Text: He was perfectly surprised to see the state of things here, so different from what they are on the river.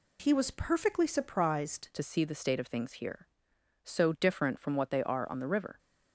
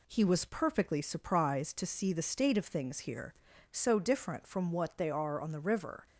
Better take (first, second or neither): second